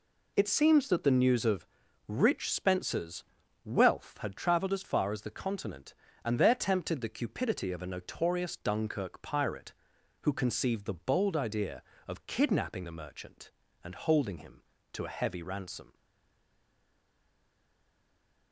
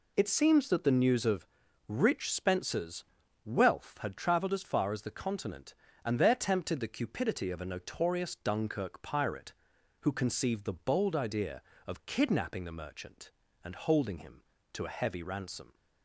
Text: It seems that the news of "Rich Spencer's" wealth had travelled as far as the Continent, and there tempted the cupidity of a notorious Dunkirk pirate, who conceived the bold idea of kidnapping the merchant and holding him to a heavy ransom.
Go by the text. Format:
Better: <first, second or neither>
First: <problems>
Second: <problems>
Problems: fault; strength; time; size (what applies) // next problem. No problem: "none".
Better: second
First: pauses between "of" and "Rich"; at 1.6 s; 0.40 s long // pauses between "Spencer's" and "wealth"; at 3.2 s; 0.40 s long // stays silent after the last word; strong; from 15.9 s on; 2.6 s long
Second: pauses between "of" and "Rich"; at 1.4 s; 0.40 s long // pauses between "Spencer's" and "wealth"; at 3.0 s; 0.40 s long